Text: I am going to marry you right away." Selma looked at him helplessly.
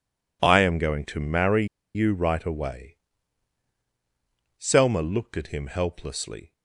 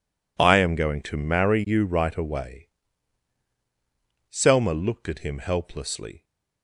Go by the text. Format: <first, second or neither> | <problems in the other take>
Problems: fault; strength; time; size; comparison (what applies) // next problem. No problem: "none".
second | pauses between "marry" and "you"; slight; at 1.6 s; 0.29 s long